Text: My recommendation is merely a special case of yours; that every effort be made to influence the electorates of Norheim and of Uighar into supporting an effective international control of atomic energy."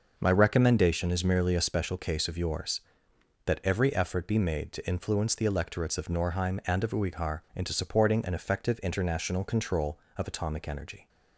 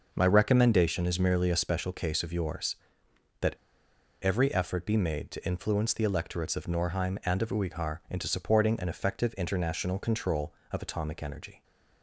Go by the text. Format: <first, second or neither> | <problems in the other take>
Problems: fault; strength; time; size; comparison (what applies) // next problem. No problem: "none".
first | pauses between "that" and "every"; noticeable; at 3.5 s; 0.65 s long